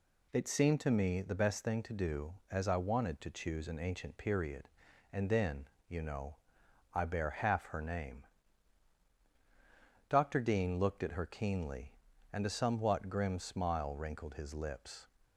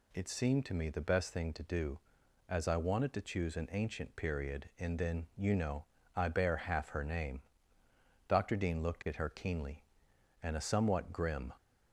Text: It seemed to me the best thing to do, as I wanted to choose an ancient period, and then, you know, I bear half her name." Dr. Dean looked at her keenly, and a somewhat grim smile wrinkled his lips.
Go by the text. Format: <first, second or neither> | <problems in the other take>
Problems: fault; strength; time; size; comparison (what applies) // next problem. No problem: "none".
first | stops before "smile wrinkled his lips"; at 11.5 s